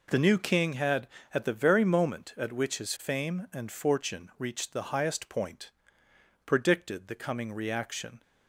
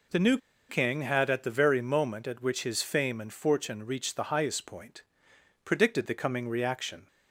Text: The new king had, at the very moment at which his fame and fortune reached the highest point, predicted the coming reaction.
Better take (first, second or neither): first